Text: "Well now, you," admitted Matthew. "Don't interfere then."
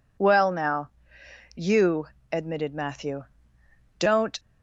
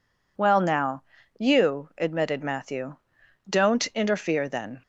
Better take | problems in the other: second | stops before "interfere then"; at 4.3 s

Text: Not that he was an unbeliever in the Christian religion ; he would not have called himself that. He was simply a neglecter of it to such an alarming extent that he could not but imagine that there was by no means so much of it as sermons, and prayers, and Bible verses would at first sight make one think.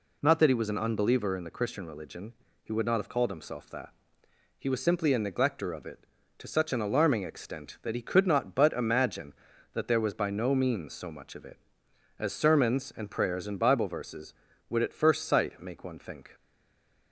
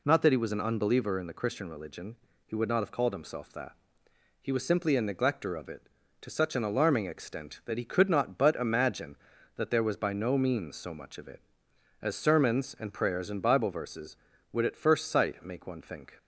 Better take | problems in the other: second | stays silent after the last word; slight; from 16.3 s on; 0.8 s long

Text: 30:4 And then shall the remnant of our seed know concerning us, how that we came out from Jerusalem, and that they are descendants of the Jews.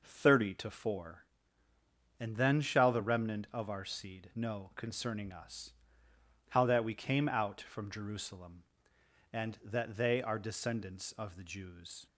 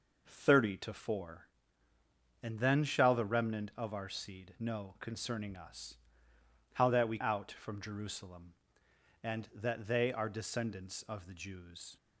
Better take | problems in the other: first | skips "came"; at 7.1 s

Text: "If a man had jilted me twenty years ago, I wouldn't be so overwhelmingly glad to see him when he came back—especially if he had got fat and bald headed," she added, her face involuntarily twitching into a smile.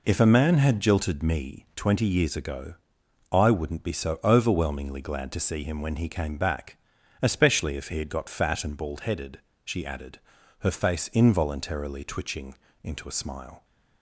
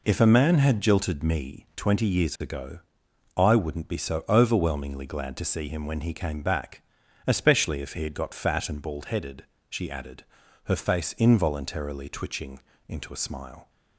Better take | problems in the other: neither | pauses between "twitching" and "into"; slight; the same in both

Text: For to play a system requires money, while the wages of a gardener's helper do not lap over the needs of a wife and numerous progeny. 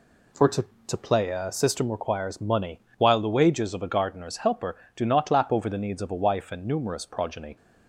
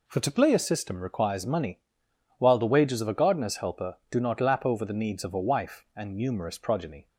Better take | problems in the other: second | says "to" twice; at 0.8 s

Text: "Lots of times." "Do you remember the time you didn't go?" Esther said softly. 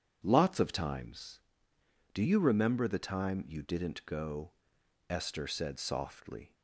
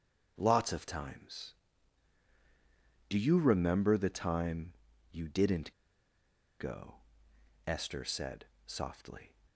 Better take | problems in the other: first | starts louder than the rest; until 1.3 s; 6.5 dB // pauses between "time" and "you"; at 4.7 s; 0.40 s long // pauses between "didn't" and "go"; noticeable; at 5.7 s; 0.87 s long // pauses between "said" and "softly"; slight; at 8.4 s; 0.20 s long

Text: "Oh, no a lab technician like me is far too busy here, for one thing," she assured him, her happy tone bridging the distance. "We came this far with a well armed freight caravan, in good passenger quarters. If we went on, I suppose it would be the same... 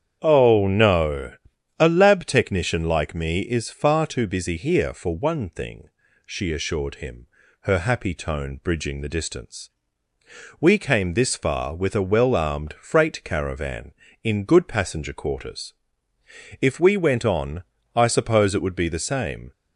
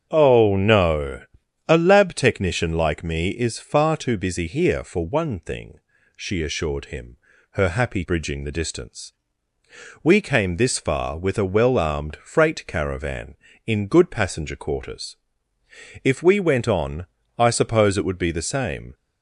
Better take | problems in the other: first | starts louder than the rest; strong; until 1.1 s; 7.5 dB; strong in the first // pauses between "no" and "a"; at 1.2 s; 0.42 s long; also in the first // skips "tone"; at 8.0 s

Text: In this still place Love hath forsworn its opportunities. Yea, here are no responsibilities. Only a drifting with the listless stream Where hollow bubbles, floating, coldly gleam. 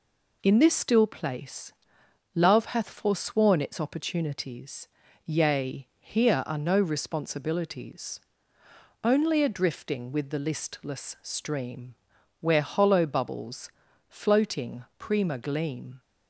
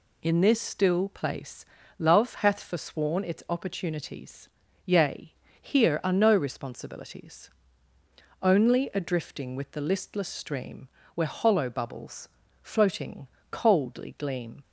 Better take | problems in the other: second | pauses between "place" and "Love"; noticeable; at 1.7 s; 0.62 s long; slight in the second // pauses between "stream" and "Where"; noticeable; at 11.9 s; 0.46 s long; slight in the second // says "prima" for "coldly"; at 14.9 s

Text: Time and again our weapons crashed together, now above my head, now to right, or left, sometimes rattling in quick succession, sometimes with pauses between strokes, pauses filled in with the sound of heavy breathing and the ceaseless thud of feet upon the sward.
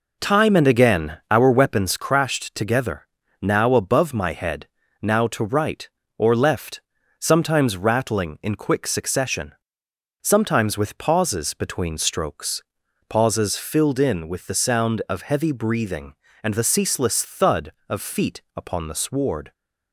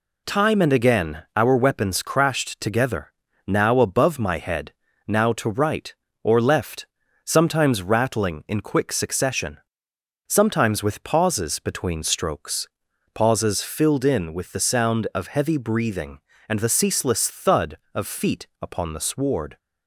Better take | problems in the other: second | starts louder than the rest; noticeable; until 2.1 s; 4 dB

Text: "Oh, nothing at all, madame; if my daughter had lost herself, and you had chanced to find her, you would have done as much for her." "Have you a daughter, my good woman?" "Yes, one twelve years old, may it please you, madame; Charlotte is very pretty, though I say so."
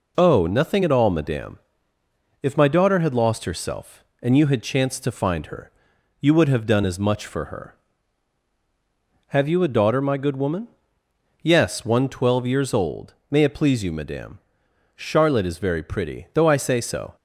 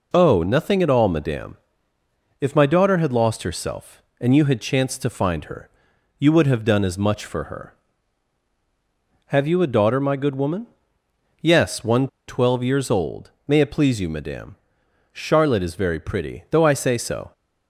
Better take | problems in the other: first | pauses between "one" and "twelve"; slight; at 12.0 s; 0.21 s long

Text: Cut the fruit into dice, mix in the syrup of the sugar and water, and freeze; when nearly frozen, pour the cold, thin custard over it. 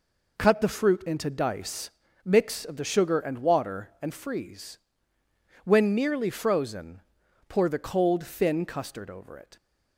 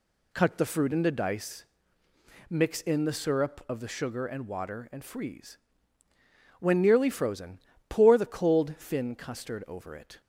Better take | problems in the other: second | skips "in the syrup"; at 2.6 s

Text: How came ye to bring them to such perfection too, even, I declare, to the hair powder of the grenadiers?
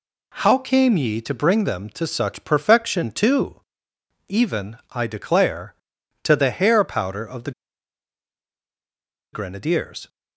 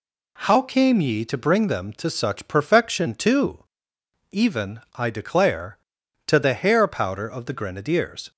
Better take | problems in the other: second | pauses between "the" and "grenadiers"; strong; at 7.5 s; 1.8 s long

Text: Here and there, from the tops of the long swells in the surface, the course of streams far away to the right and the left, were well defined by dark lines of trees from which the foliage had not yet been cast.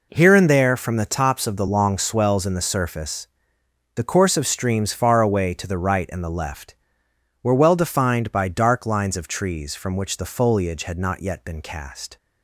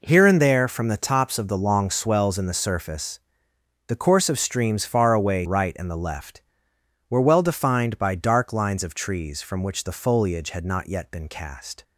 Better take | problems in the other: first | skips "to the"; at 5.4 s

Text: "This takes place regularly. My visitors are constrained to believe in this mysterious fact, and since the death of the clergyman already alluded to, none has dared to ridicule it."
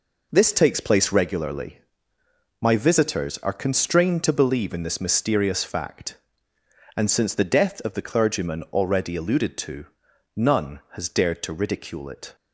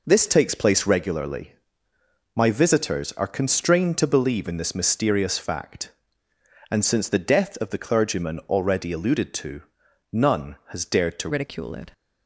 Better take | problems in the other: first | changes voice at "ridicule"; from 11.2 s on; 0.7 s long

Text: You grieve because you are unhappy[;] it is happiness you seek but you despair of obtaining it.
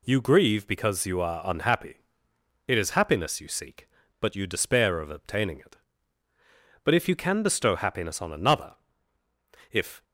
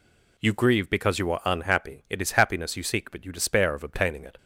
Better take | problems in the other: second | goes on to say "But if you can bestow happiness on another if"; strong; from 6.8 s on; 3.2 s long

